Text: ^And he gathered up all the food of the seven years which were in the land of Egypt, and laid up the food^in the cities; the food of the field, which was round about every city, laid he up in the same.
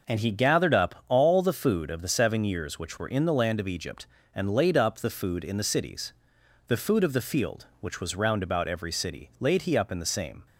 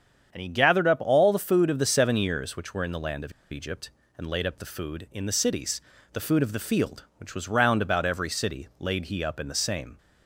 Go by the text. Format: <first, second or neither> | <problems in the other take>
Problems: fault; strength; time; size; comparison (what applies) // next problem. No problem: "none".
first | starts louder than the rest; strong; until 1.3 s; 8 dB // pauses between "of" and "Egypt"; slight; at 3.3 s; 0.19 s long